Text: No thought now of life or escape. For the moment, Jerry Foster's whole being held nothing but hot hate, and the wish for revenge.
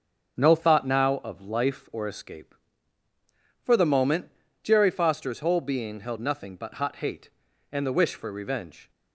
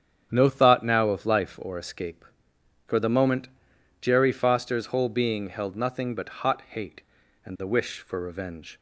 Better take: neither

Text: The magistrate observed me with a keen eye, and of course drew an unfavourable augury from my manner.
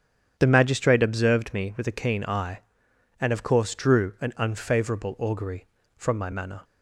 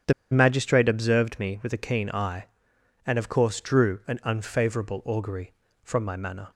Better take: first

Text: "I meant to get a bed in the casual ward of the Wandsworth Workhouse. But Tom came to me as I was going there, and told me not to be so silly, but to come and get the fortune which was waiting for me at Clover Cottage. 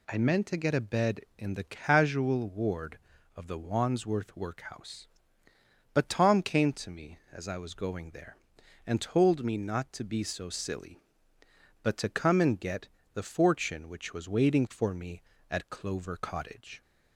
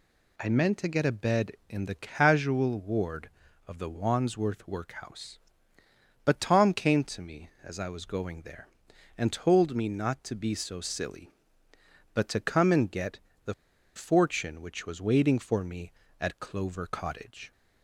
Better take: first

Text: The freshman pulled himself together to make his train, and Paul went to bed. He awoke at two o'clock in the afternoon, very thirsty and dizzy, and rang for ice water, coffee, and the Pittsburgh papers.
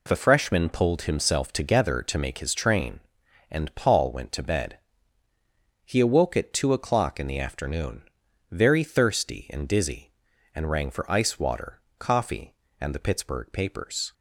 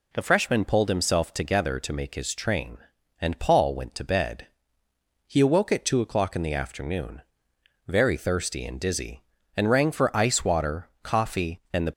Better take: first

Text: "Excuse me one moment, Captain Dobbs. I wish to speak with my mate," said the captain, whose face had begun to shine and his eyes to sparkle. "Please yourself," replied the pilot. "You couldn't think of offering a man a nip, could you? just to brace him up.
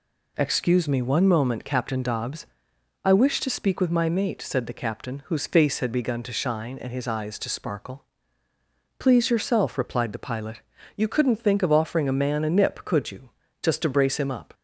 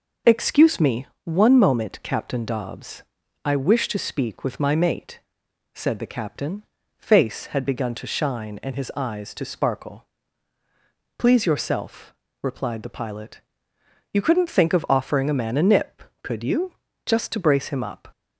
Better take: first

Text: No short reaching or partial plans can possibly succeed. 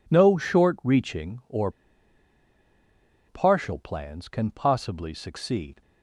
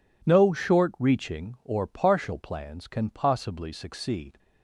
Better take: second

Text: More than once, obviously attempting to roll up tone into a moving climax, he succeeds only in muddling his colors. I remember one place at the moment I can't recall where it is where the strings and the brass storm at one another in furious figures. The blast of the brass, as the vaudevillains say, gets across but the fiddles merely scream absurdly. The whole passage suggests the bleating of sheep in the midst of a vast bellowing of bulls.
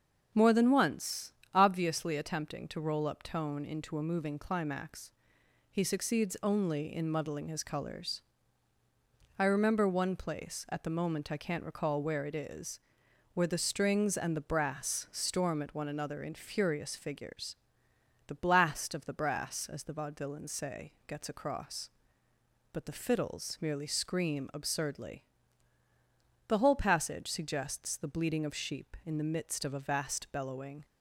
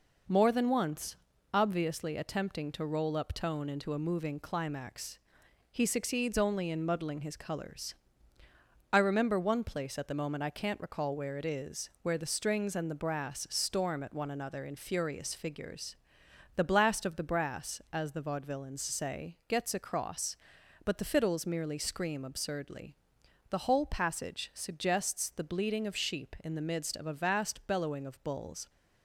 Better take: second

